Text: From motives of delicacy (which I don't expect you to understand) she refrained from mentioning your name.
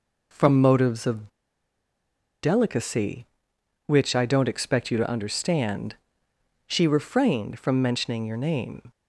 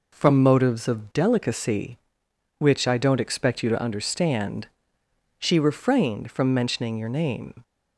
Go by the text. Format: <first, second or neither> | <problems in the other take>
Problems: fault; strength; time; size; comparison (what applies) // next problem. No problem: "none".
second | pauses between "of" and "delicacy"; at 1.2 s; 1.1 s long